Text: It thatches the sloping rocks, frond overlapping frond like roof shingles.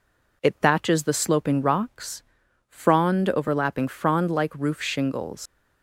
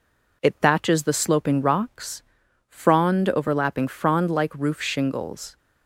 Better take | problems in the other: second | leaves "shingles" unfinished; at 5.4 s; 115 ms

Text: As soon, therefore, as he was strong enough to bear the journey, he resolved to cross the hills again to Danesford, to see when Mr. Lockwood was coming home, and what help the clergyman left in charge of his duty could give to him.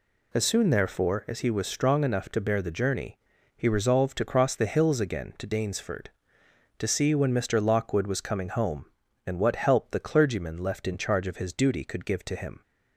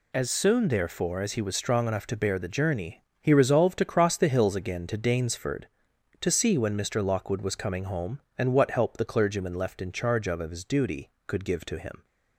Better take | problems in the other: first | says "of" twice; at 10.4 s

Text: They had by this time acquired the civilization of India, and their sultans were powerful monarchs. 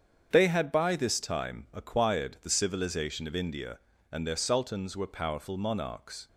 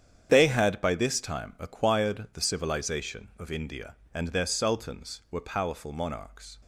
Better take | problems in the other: neither | starts louder than the rest; strong; the same in both

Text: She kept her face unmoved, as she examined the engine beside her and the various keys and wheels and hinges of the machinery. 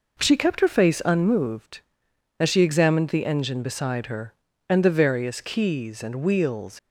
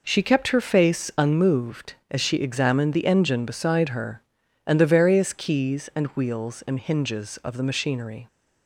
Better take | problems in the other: second | stops before "and hinges of the machinery"; at 6.7 s

